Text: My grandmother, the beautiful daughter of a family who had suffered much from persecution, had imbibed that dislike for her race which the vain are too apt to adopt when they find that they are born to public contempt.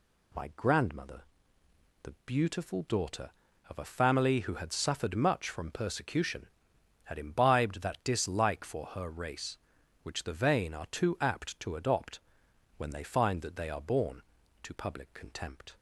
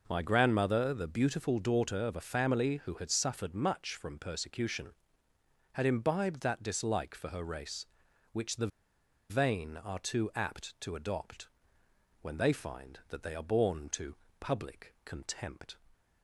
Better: first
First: pauses between "adopt" and "when"; noticeable; at 12.1 s; 0.58 s long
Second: pauses between "the" and "vain"; noticeable; at 8.6 s; 0.61 s long // pauses between "adopt" and "when"; noticeable; at 11.4 s; 0.72 s long // pauses between "to" and "public"; slight; at 14.1 s; 0.24 s long

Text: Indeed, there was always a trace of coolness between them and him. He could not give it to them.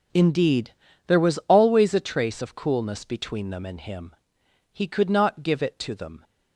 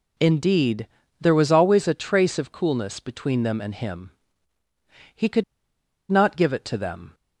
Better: first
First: none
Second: pauses between "could" and "not"; noticeable; at 5.4 s; 0.68 s long

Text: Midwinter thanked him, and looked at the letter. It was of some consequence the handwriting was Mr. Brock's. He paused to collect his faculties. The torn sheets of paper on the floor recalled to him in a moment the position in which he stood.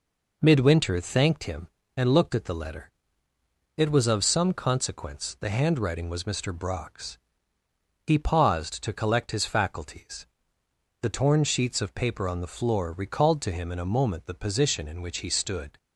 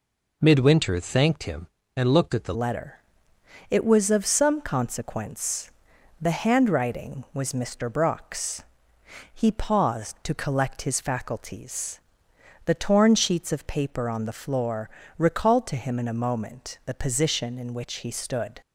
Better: first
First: none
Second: changes voice at "letter"; from 2.5 s on; 16.0 s long // pauses between "consequence" and "the"; noticeable; at 5.6 s; 0.50 s long // pauses between "floor" and "recalled"; slight; at 14.8 s; 0.28 s long

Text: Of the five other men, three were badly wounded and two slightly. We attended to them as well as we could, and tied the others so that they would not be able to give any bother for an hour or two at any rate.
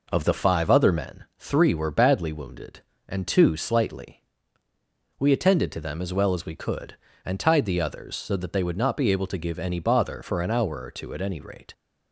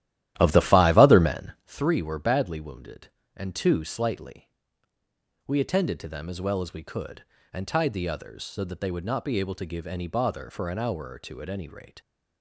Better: first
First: none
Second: starts louder than the rest; strong; until 1.7 s; 13.5 dB

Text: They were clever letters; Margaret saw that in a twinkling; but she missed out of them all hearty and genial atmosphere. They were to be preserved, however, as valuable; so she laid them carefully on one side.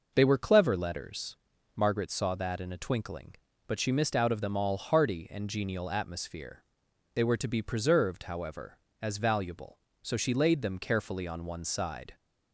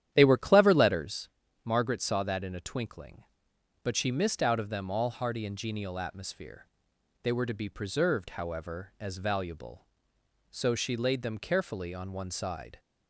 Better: first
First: none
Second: starts louder than the rest; strong; until 1.2 s; 11 dB

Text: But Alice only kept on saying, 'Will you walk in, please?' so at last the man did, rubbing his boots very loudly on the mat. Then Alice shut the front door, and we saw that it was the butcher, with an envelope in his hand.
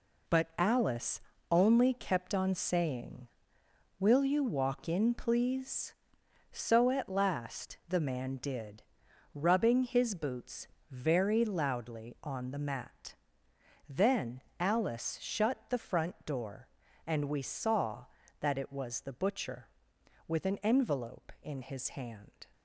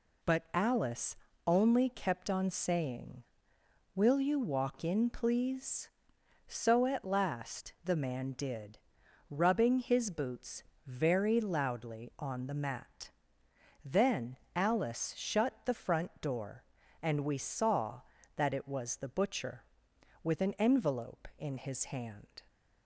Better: second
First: gets quieter; strong; throughout; 9 dB // pauses between "Alice" and "only"; slight; at 1.1 s; 0.30 s long // pauses between "boots" and "very"; slight; at 10.6 s; 0.24 s long // pauses between "Then" and "Alice"; slight; at 14.4 s; 0.16 s long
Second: pauses between "Alice" and "only"; slight; at 1.1 s; 0.30 s long // pauses between "boots" and "very"; slight; at 10.6 s; 0.24 s long // pauses between "Then" and "Alice"; slight; at 14.3 s; 0.16 s long

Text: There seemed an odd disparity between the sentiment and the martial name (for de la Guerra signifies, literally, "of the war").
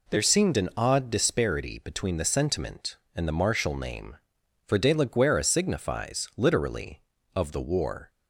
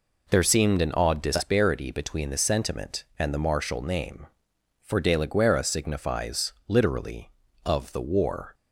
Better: neither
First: none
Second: none

